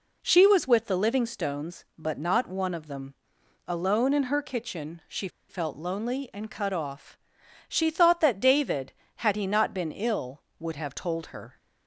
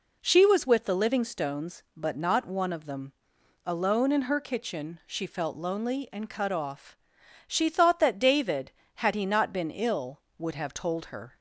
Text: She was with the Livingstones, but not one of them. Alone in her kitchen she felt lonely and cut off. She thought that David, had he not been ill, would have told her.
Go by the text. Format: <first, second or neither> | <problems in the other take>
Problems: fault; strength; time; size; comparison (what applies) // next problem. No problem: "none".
second | pauses between "she" and "felt"; slight; at 5.2 s; 0.20 s long